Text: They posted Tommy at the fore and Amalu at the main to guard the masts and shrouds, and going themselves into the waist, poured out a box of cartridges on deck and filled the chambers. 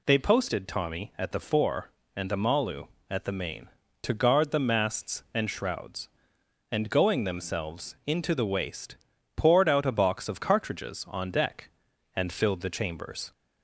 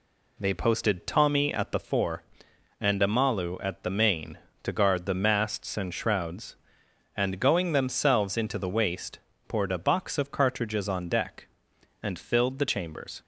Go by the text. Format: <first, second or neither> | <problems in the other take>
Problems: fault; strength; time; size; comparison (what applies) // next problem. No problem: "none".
first | skips "out"; at 9.7 s